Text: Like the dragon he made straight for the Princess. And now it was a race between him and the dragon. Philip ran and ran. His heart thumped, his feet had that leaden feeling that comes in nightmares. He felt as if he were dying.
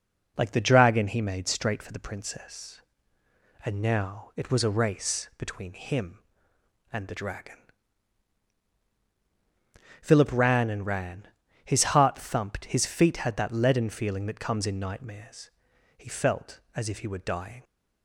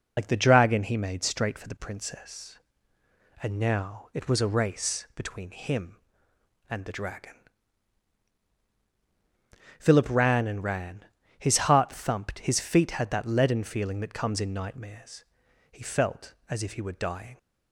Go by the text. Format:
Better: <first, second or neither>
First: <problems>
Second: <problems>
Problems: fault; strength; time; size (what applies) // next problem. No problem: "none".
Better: first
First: none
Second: loses the start of "Like"; at 0.1 s; 55 ms